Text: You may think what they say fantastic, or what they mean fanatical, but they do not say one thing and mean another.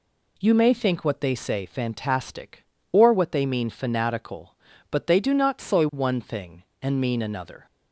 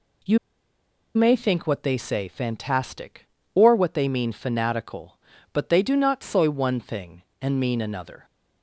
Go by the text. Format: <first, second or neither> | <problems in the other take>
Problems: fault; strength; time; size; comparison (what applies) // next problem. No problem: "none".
first | pauses between "You" and "may"; noticeable; at 0.3 s; 0.77 s long